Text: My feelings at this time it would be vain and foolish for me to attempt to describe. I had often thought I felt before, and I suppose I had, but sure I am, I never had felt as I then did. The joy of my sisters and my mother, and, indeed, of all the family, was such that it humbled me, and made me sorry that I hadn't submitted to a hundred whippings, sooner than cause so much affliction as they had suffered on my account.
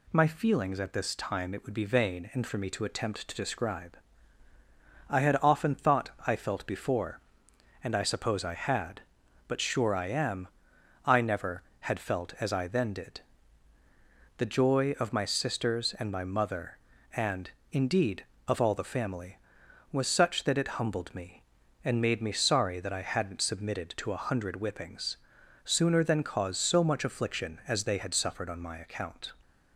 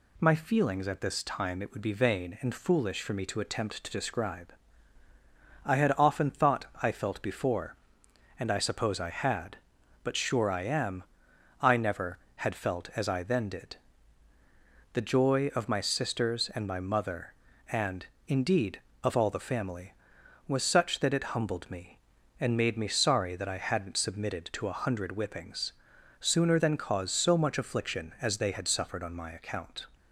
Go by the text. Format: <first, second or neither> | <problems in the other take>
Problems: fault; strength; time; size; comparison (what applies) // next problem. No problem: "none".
second | skips "foolish"; at 2.4 s // pauses between "thought" and "I"; slight; at 6.0 s; 0.16 s long; slight in the second